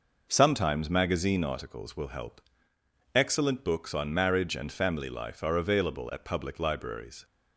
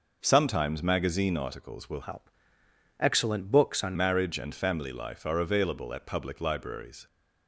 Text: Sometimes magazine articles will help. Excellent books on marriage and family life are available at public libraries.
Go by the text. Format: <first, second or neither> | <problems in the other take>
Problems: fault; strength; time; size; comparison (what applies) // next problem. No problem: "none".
first | changes voice from "help" to "on"; from 2.0 to 3.9 s; 1.9 s long